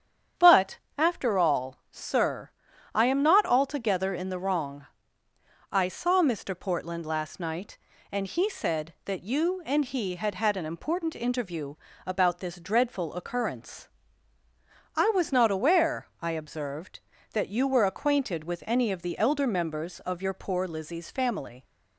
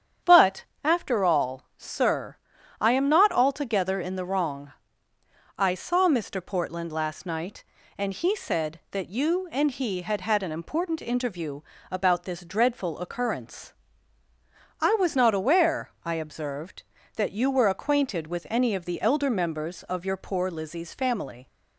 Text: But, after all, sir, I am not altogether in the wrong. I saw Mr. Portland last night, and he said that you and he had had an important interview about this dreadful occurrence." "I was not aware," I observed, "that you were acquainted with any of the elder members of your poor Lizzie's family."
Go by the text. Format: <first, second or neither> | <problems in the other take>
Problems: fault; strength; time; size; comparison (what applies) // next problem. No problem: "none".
neither | starts louder than the rest; strong; the same in both // pauses between "interview" and "about"; slight; the same in both